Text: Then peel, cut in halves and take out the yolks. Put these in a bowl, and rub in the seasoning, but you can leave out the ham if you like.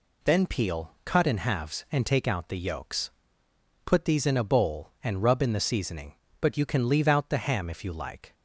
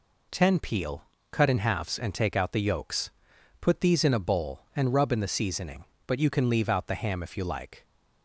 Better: first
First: none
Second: says "Ten" for "Then"; at 0.2 s

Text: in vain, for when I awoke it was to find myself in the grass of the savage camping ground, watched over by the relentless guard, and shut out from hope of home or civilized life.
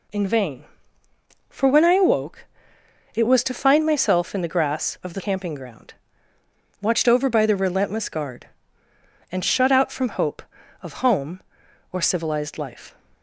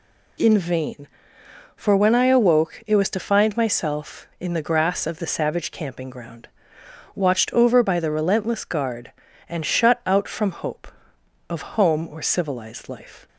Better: second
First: pauses between "awoke" and "it"; noticeable; at 2.4 s; 0.70 s long // skips "savage"; at 5.1 s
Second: none

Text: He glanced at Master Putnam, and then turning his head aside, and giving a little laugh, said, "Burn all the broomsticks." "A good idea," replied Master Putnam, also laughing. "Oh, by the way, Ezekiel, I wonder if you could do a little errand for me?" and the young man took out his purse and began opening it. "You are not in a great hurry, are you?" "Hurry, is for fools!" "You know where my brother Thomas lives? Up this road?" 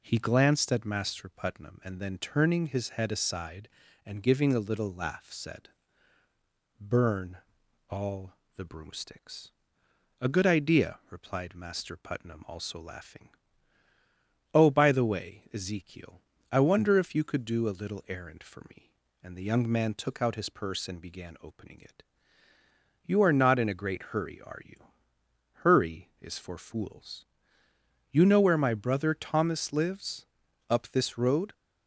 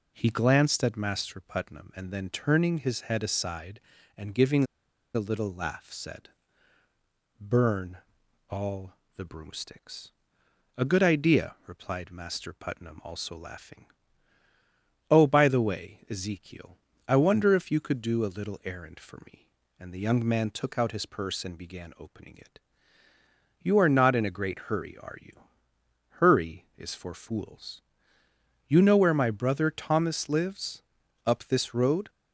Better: first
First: pauses between "Burn" and "all"; noticeable; at 7.3 s; 0.52 s long // pauses between "all" and "the"; slight; at 8.3 s; 0.20 s long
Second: pauses between "giving" and "a"; noticeable; at 4.6 s; 0.50 s long // pauses between "Burn" and "all"; noticeable; at 7.9 s; 0.52 s long // pauses between "all" and "the"; slight; at 8.9 s; 0.20 s long

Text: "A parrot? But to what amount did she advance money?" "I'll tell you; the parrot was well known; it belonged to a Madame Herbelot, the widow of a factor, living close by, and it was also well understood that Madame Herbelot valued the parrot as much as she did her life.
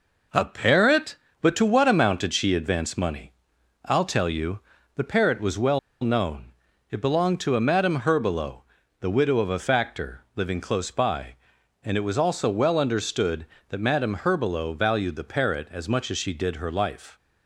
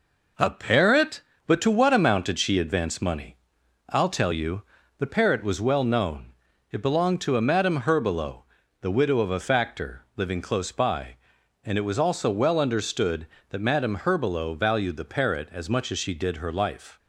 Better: second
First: pauses between "well" and "known"; slight; at 5.7 s; 0.23 s long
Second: none

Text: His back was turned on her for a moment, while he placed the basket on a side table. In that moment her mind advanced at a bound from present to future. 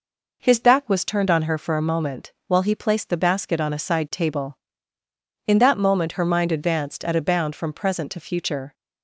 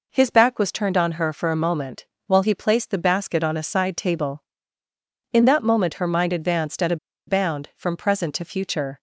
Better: first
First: none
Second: pauses between "a" and "bound"; slight; at 6.9 s; 0.31 s long

